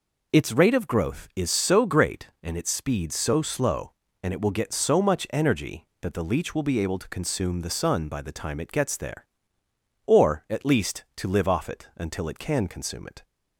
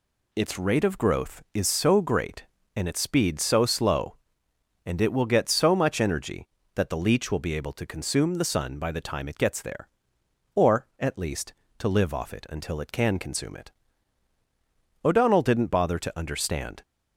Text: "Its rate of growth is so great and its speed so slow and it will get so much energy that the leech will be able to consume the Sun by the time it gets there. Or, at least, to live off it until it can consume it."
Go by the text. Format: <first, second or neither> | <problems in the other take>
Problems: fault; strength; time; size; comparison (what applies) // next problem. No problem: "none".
first | goes on to say "O'Donnell didn't bother to understand"; strong; from 15.0 s on; 1.7 s long